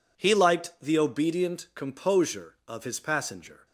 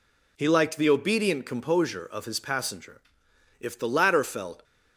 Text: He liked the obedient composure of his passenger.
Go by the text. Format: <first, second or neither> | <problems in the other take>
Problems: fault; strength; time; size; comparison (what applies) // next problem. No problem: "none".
first | goes on to say "If the latter felt"; noticeable; from 3.5 s on; 1.0 s long